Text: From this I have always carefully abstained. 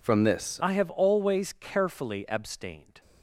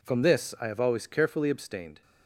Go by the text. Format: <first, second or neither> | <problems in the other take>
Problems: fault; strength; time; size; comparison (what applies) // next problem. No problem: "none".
second | changes voice at "I"; from 0.6 s on; 2.4 s long